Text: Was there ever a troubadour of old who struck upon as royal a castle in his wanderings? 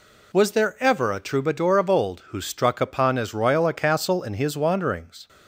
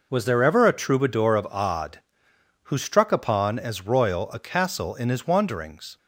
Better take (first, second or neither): first